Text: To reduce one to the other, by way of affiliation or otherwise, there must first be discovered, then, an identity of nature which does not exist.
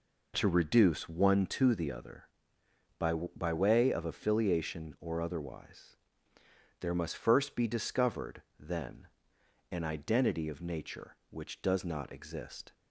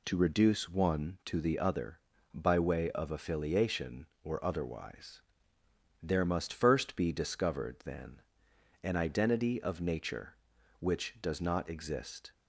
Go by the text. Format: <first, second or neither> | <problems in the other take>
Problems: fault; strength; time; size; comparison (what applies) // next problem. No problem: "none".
second | says "by" twice; at 3.1 s